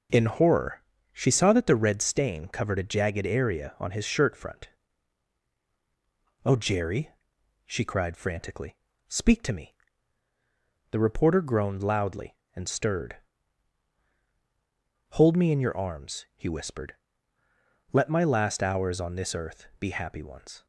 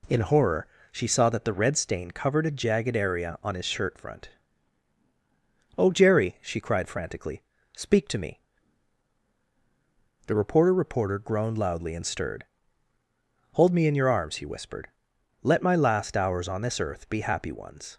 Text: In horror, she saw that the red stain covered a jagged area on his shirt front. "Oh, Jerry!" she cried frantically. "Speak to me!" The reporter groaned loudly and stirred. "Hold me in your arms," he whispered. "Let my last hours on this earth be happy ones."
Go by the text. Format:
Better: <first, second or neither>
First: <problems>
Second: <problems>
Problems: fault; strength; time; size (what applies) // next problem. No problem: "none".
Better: first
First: none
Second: says "reporter" twice; at 10.7 s